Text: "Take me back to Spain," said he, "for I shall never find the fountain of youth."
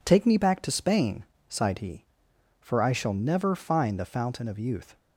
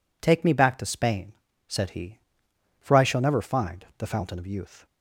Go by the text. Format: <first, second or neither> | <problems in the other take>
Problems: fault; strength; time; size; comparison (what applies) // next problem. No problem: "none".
second | says "sighed" for "said"; at 1.4 s